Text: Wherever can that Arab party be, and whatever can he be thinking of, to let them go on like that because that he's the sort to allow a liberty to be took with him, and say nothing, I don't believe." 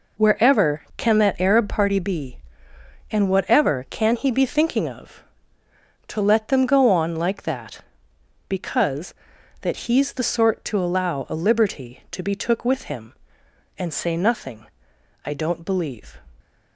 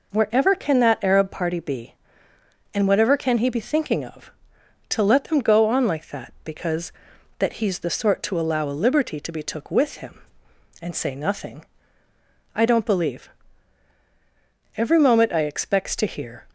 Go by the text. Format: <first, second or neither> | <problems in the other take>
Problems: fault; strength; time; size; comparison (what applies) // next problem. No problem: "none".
first | goes on to say "Every moment I expects to hear"; strong; from 14.7 s on; 1.7 s long